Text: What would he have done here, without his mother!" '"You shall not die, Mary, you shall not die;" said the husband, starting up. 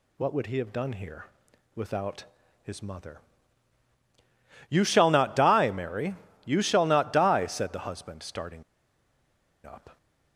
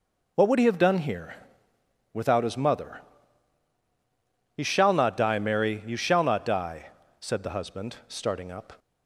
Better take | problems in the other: second | pauses between "without" and "his"; at 2.2 s; 0.40 s long // pauses between "starting" and "up"; at 8.6 s; 1.0 s long

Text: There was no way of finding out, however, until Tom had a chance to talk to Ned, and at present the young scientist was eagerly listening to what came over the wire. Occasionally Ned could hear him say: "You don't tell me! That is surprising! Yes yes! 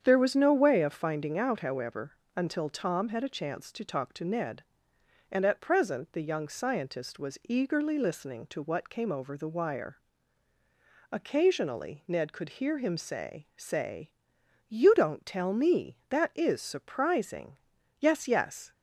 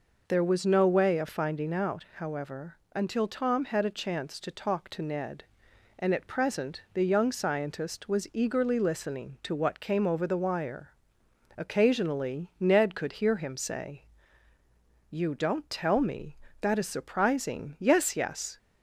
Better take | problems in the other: second | starts louder than the rest; strong; until 1.0 s; 8 dB // says "say" twice; at 13.5 s

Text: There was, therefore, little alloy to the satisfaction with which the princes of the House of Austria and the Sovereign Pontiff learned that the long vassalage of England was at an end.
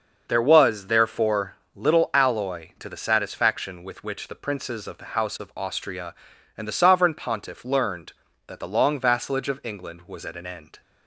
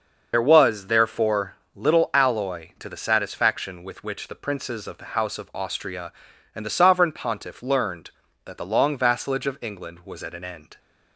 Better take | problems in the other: first | loses the start of "There"; at 0.3 s; 50 ms

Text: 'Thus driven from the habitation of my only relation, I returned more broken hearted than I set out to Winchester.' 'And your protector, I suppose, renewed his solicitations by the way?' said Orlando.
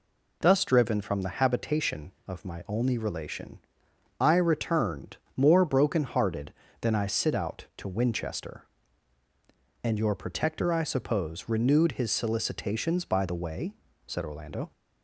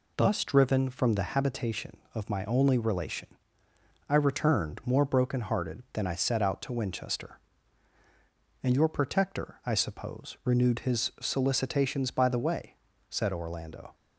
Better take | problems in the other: second | pauses between "returned" and "more"; slight; at 5.1 s; 0.18 s long // says "sit" for "set"; at 7.0 s

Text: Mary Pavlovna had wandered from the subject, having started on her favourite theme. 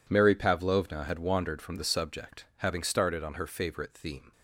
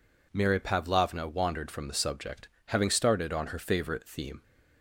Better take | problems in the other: first | skips "had"; at 1.2 s

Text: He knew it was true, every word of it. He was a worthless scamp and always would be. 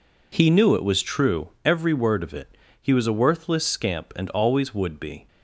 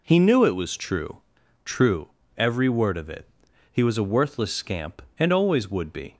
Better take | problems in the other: first | says "true" twice; at 1.6 s

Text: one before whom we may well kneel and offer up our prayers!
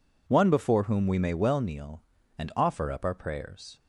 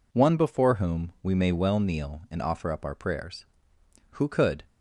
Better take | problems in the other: first | goes on to say "Who could"; from 4.1 s on; 0.50 s long

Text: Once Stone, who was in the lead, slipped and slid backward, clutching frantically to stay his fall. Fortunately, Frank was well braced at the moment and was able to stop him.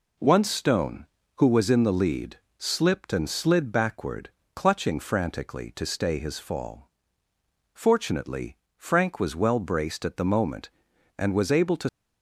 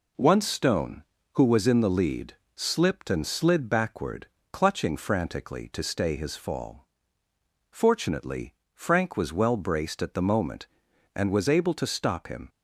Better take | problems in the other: second | stops before "stop him"; at 11.8 s

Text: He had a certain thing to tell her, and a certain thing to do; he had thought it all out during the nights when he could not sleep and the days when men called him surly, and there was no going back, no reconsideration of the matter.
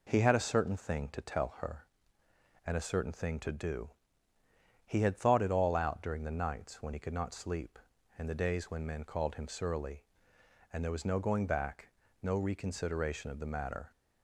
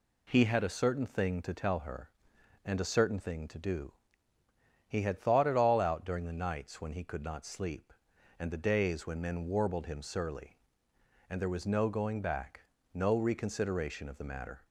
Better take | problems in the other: first | says "warbled" for "called"; at 9.4 s

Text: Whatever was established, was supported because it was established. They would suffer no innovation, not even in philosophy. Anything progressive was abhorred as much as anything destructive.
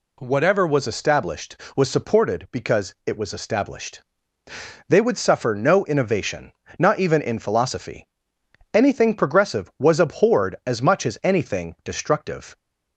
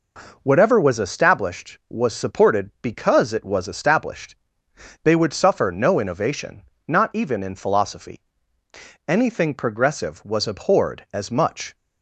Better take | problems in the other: first | stops before "as anything destructive"; at 11.7 s

